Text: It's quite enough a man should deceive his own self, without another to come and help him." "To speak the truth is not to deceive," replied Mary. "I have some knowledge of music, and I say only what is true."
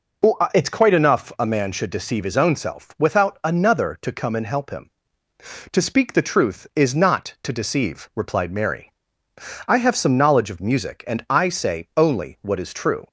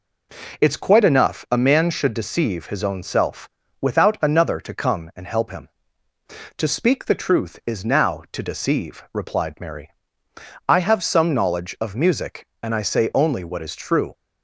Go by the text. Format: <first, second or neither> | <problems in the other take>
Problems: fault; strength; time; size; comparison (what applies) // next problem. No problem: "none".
first | says "now" for "not"; at 7.8 s